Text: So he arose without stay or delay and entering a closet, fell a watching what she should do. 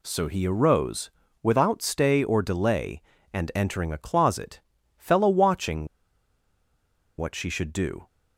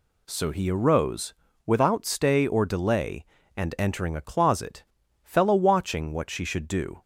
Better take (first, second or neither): second